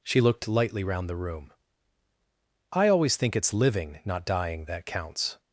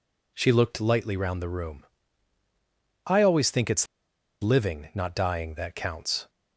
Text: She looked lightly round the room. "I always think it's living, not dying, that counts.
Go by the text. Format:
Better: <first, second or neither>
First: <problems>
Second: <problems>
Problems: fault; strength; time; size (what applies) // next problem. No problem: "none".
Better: first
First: none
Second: pauses between "it's" and "living"; noticeable; at 3.8 s; 0.55 s long